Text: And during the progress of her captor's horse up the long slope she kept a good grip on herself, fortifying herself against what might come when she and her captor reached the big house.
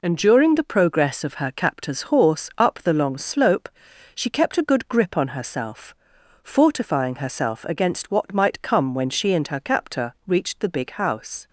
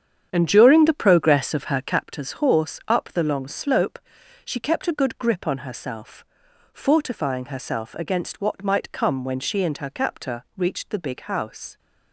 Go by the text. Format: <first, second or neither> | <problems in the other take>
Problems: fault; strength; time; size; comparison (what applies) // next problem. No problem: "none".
first | starts louder than the rest; strong; until 2.0 s; 8.5 dB // pauses between "slope" and "she"; noticeable; at 3.9 s; 0.46 s long; noticeable in the first